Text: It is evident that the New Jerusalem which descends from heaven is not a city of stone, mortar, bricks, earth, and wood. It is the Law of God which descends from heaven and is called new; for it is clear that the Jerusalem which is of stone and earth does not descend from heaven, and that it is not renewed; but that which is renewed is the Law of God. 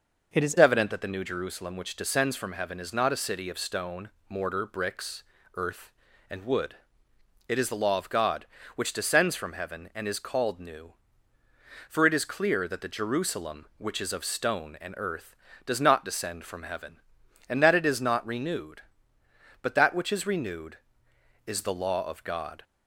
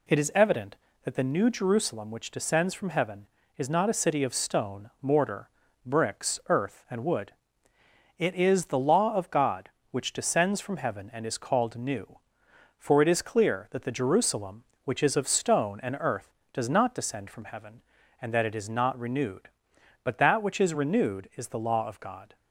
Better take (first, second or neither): second